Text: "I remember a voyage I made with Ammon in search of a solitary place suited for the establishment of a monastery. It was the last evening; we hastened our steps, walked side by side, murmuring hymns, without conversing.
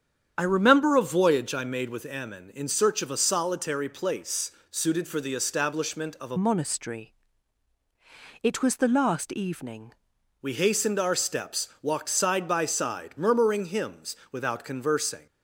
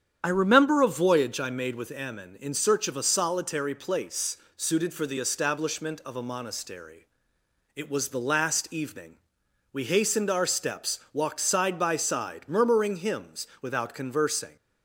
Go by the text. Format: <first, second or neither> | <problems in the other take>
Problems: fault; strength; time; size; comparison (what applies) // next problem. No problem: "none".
second | starts louder than the rest; strong; until 1.3 s; 8.5 dB; strong in the second // pauses between "place" and "suited"; slight; at 4.4 s; 0.20 s long; slight in the second // changes voice from "monastery" to "evening"; from 6.3 to 9.9 s; 3.6 s long